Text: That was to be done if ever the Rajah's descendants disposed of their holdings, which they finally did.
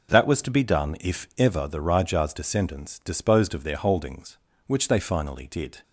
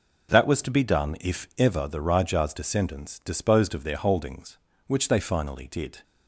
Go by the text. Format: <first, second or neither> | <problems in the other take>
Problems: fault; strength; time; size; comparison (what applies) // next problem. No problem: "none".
neither | none